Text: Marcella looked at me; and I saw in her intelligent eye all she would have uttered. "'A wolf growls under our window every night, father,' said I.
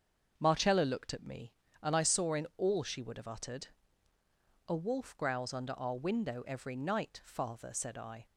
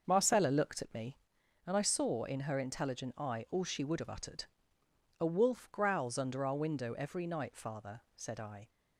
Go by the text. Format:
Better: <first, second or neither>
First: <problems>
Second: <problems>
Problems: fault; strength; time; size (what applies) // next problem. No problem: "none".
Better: second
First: starts louder than the rest; until 1.3 s; 7 dB // skips "her intelligent eye"; at 2.5 s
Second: starts louder than the rest; until 1.0 s; 6 dB